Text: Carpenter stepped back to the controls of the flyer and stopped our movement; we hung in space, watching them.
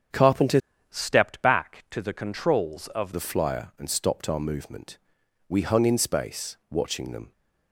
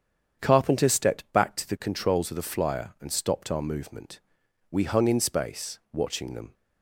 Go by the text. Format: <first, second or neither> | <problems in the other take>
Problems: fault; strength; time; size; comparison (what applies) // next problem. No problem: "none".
second | starts louder than the rest; strong; until 1.4 s; 7.5 dB; strong in the second // changes voice from "stepped" to "of"; from 0.8 to 3.1 s; 2.3 s long